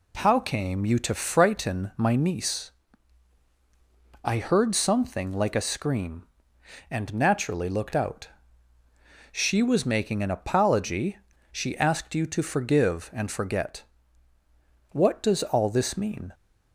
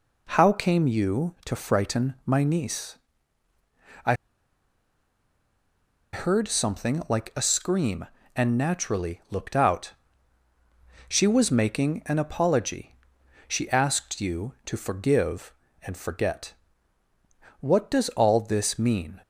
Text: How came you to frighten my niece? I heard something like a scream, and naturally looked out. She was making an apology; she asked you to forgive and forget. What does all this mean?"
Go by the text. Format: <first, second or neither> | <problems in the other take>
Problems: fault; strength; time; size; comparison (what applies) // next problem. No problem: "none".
first | pauses between "I" and "heard"; strong; at 4.1 s; 1.9 s long